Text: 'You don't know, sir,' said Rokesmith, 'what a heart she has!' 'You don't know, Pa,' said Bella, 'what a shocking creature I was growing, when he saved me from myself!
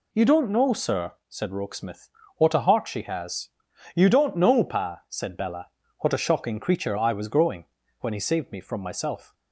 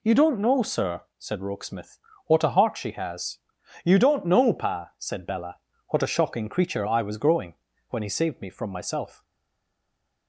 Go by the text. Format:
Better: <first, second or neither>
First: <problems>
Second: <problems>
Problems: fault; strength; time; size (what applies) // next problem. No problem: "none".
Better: first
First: none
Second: stays silent after the last word; from 9.2 s on; 1.0 s long